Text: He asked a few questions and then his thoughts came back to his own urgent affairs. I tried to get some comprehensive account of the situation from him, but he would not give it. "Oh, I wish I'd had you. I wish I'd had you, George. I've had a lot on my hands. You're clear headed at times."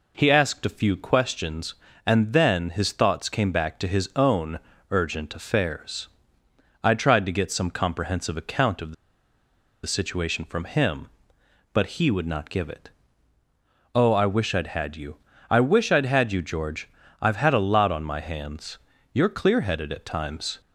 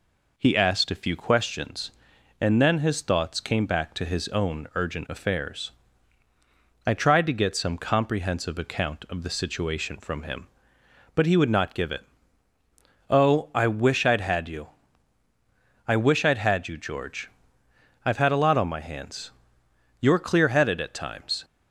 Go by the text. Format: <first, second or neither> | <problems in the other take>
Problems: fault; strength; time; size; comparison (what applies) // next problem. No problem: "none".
second | pauses between "own" and "urgent"; slight; at 4.5 s; 0.30 s long // pauses between "the" and "situation"; noticeable; at 8.9 s; 0.91 s long